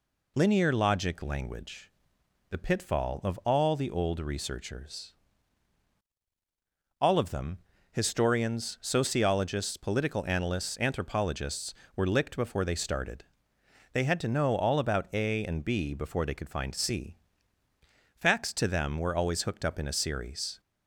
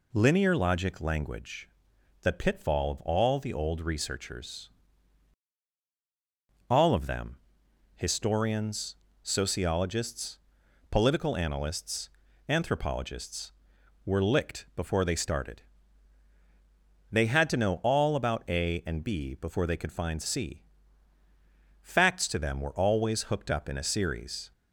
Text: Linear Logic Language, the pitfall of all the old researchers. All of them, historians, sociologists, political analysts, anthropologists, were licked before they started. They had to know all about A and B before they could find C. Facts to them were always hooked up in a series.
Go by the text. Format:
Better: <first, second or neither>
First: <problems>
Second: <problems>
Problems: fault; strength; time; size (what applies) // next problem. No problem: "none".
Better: neither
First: none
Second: none